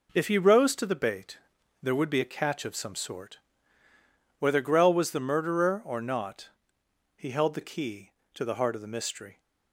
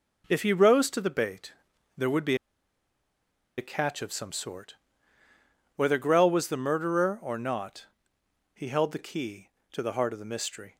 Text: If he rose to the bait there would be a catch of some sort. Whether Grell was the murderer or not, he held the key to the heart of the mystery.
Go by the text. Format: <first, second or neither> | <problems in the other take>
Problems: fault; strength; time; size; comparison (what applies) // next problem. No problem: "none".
first | pauses between "bait" and "there"; noticeable; at 1.5 s; 0.46 s long; noticeable in the first // pauses between "be" and "a"; at 2.3 s; 1.2 s long